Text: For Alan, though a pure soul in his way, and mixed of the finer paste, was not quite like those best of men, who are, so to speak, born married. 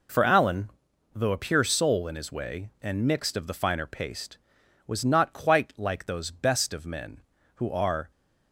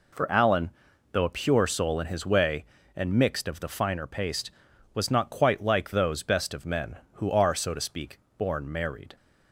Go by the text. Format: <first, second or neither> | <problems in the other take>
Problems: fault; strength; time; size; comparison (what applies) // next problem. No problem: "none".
second | stops before "so to speak born married"; at 8.1 s